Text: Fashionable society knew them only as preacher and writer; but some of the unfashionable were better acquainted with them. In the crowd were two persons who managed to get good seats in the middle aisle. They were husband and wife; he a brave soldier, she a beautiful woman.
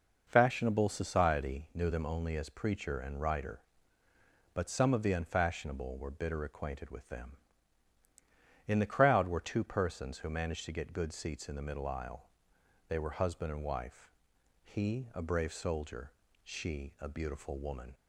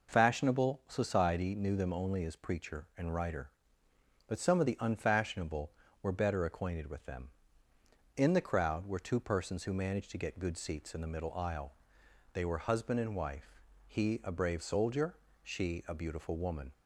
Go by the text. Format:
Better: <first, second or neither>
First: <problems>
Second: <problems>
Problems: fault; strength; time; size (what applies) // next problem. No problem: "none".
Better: second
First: says "bitter" for "better"; at 6.0 s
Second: none